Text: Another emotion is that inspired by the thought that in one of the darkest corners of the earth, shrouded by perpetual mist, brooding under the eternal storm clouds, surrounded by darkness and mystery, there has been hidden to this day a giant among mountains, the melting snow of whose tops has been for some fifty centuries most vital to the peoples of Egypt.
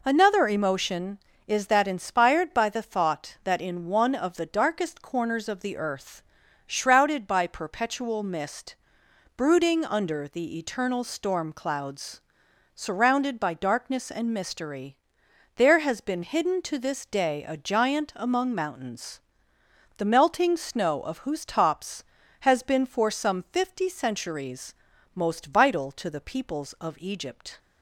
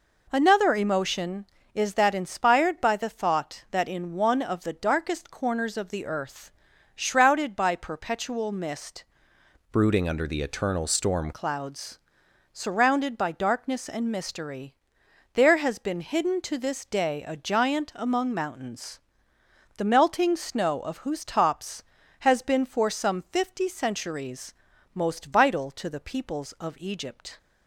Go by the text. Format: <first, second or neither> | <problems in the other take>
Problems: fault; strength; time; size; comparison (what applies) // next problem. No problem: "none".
first | changes voice from "brooding" to "storm"; from 9.7 to 11.3 s; 1.6 s long // pauses between "centuries" and "most"; at 24.5 s; 0.40 s long; also in the first